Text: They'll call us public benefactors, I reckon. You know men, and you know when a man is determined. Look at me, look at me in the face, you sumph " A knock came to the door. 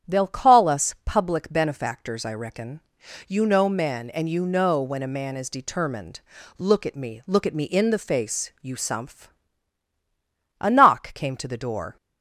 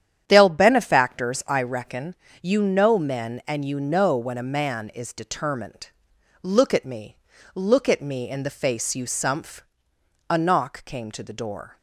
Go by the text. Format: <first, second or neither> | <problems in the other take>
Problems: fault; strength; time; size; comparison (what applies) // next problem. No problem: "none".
first | starts louder than the rest; strong; until 1.2 s; 9.5 dB; strong in the first // skips "call us public"; at 0.4 s